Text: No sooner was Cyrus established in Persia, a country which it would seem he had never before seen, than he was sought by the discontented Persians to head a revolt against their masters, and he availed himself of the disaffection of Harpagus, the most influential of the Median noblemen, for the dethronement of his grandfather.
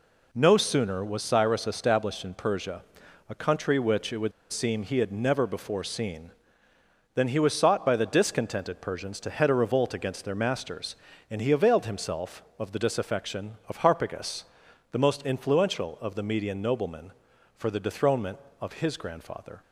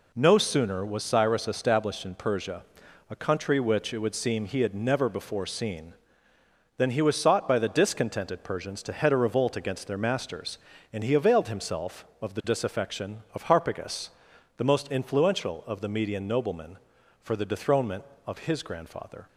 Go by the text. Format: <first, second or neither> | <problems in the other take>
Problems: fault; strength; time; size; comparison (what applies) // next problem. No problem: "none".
second | pauses between "would" and "seem"; slight; at 4.3 s; 0.20 s long